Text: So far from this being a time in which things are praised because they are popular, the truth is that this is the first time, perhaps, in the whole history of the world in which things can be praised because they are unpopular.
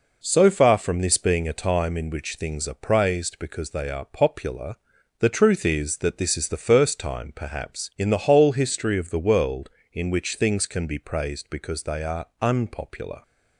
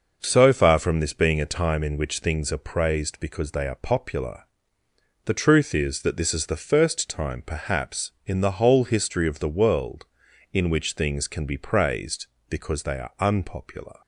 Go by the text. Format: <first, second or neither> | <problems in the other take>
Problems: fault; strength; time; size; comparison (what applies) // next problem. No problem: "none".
neither | none